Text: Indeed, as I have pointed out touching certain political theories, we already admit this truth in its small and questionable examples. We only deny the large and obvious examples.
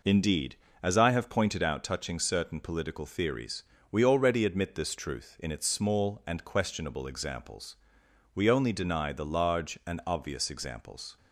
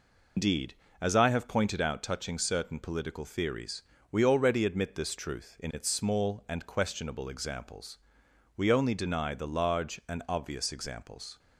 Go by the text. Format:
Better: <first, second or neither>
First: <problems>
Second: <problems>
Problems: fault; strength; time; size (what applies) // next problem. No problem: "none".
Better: first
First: none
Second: loses the start of "Indeed"; at 0.3 s; 140 ms